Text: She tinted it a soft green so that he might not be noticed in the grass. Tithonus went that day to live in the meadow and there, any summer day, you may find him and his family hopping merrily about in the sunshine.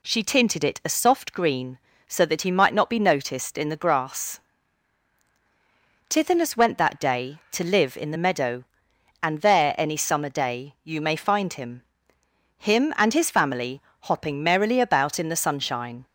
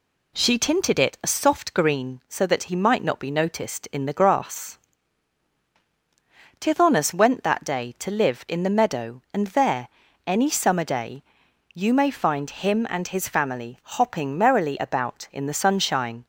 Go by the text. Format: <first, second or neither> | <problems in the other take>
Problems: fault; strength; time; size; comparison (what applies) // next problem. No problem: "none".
second | says "him" twice; at 12.5 s // pauses between "family" and "hopping"; slight; at 13.8 s; 0.20 s long